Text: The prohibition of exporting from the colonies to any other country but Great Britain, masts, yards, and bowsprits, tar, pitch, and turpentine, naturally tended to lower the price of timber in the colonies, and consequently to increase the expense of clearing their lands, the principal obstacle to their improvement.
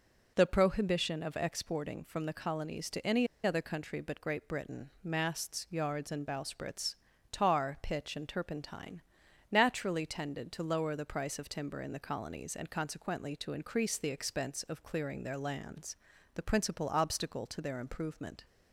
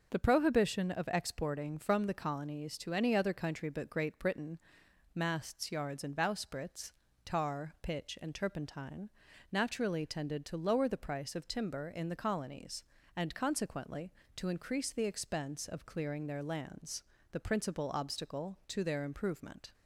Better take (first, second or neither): second